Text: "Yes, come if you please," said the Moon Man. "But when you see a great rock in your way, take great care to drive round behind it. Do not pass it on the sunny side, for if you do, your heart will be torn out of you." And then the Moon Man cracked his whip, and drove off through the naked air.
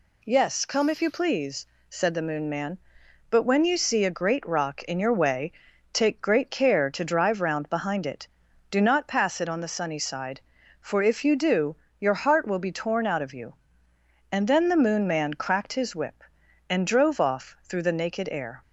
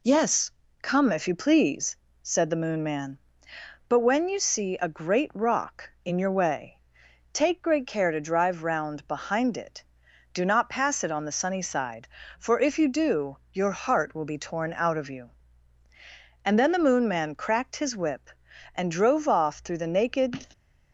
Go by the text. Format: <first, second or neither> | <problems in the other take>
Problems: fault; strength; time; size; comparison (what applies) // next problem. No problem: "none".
first | stops before "air"; at 20.5 s